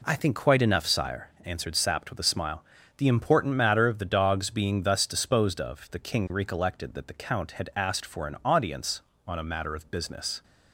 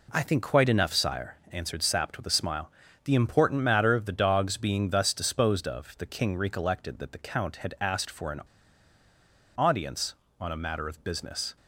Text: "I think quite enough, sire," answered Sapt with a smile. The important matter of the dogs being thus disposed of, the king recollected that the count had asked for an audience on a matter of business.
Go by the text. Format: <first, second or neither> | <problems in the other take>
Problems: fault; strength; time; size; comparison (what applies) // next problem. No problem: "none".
first | pauses between "an" and "audience"; at 8.4 s; 1.1 s long